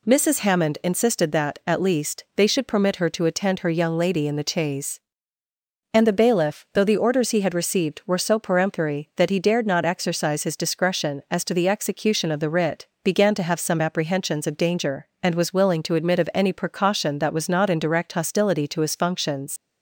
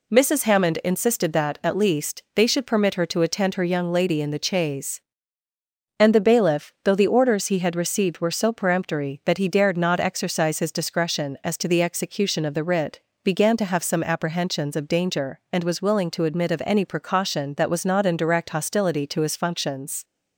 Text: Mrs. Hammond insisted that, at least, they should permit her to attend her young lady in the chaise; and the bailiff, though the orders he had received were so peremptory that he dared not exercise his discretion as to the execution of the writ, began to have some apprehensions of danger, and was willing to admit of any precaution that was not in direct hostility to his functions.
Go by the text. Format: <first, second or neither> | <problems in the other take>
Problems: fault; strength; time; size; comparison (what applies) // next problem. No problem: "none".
second | leaves "functions" unfinished; at 19.5 s; 100 ms